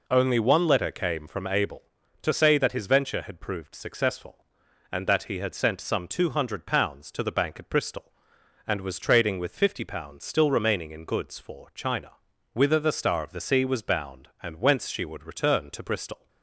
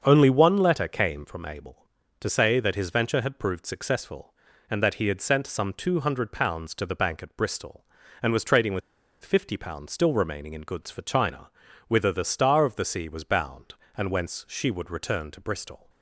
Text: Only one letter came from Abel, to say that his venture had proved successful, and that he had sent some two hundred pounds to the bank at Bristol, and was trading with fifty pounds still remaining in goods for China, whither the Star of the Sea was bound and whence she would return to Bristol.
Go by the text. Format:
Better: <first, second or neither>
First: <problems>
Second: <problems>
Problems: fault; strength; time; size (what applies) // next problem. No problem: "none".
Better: first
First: none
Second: starts louder than the rest; until 1.0 s; 7 dB // pauses between "with" and "fifty"; at 8.8 s; 0.42 s long